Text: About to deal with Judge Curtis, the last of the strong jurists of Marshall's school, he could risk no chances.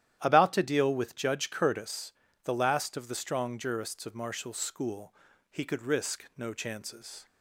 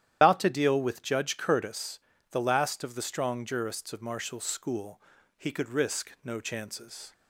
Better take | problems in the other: first | loses the start of "About"; at 0.2 s; 135 ms // starts louder than the rest; strong; until 1.2 s; 10.5 dB; strong in the first

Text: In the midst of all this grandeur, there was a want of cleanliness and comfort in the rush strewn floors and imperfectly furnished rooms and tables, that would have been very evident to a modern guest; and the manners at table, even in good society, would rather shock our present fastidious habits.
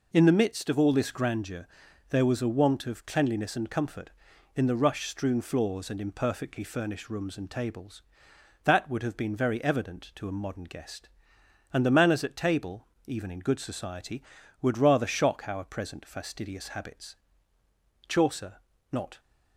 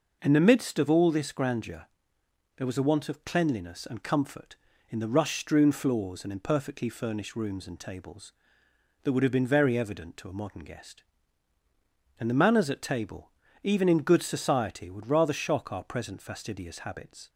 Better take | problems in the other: second | goes on to say "Chaucer not"; noticeable; from 18.0 s on; 1.1 s long

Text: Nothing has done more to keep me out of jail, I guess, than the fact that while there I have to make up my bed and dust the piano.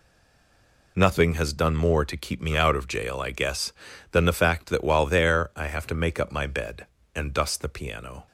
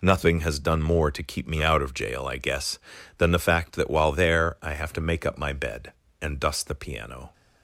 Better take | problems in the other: second | stays silent before the first word; slight; until 0.9 s; 0.9 s long

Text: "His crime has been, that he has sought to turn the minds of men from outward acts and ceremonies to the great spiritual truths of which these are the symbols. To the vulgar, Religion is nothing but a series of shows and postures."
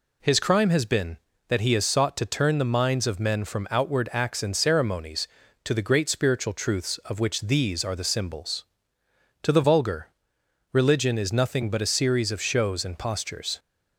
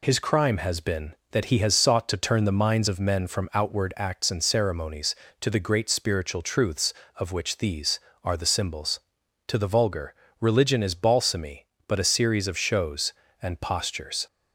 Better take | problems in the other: first | says "balsamy" for "nothing"; at 10.9 s

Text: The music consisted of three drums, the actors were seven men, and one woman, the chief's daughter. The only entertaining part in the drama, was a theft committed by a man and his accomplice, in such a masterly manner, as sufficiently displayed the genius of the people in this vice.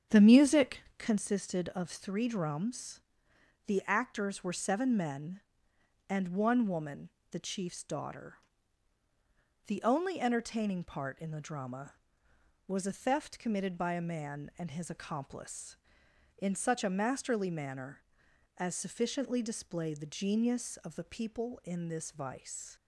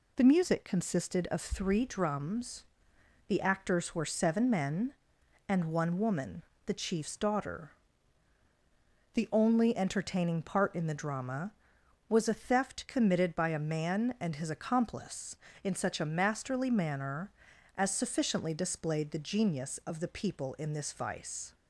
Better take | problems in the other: second | starts louder than the rest; strong; until 1.2 s; 8 dB // pauses between "music" and "consisted"; slight; at 0.8 s; 0.16 s long

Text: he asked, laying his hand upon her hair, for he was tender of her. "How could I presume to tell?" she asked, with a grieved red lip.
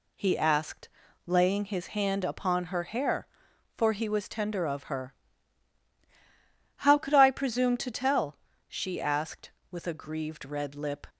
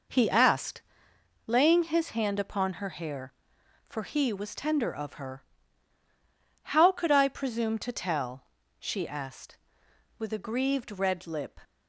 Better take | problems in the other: first | starts louder than the rest; noticeable; until 1.3 s; 5 dB

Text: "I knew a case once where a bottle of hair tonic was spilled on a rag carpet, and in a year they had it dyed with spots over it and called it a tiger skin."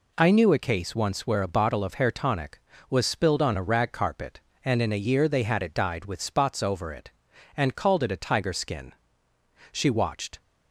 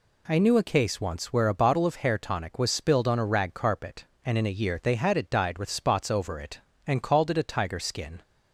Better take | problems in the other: second | goes on to say "She watched"; noticeable; from 9.7 s on; 0.68 s long

